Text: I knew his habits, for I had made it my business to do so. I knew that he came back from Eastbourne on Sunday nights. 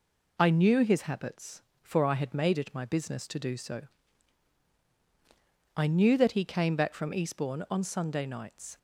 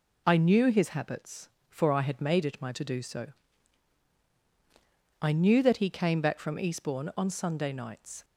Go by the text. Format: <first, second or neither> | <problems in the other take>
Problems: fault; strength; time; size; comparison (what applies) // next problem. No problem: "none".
first | skips "business"; at 2.7 s